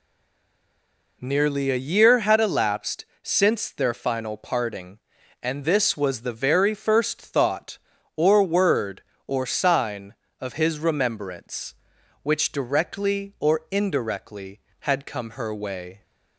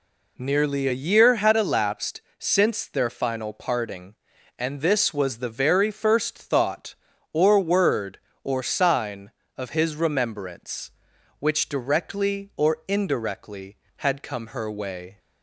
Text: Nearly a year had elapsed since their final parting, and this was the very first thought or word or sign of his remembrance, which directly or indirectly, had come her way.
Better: second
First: stays silent before the first word; noticeable; until 1.2 s; 1.2 s long // pauses between "elapsed" and "since"; slight; at 3.0 s; 0.18 s long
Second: pauses between "elapsed" and "since"; slight; at 2.2 s; 0.18 s long

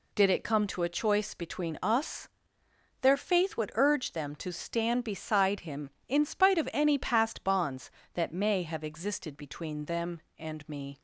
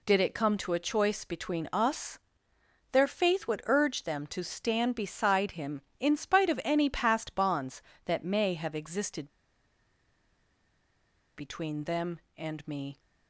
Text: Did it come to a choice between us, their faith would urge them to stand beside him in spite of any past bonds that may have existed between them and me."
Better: first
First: none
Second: pauses between "existed" and "between"; strong; at 9.2 s; 2.0 s long

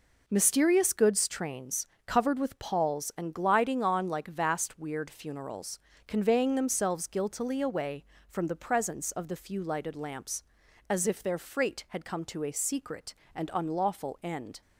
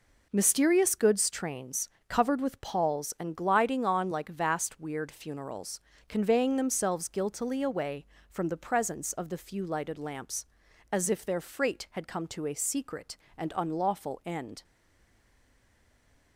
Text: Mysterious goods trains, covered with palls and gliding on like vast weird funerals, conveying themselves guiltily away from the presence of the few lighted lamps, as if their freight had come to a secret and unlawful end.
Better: first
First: none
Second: stays silent after the last word; noticeable; from 14.6 s on; 1.7 s long

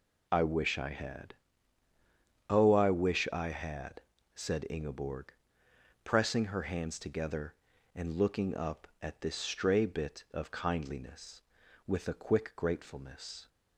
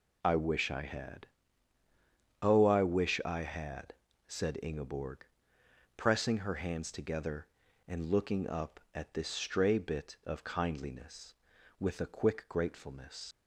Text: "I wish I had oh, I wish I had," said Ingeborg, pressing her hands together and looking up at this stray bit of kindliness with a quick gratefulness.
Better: first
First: pauses between "had" and "oh"; at 1.3 s; 1.1 s long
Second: pauses between "had" and "oh"; at 1.2 s; 1.1 s long // leaves "gratefulness" unfinished; at 13.3 s; 95 ms

